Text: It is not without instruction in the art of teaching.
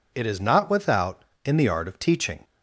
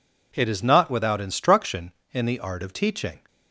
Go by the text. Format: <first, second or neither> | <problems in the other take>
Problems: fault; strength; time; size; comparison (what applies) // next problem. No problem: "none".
second | skips "instruction"; at 1.3 s